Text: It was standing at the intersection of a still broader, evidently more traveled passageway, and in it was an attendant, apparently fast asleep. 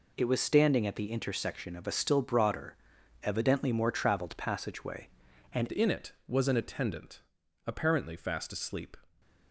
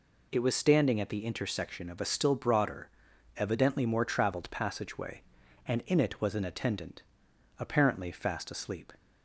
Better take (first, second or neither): second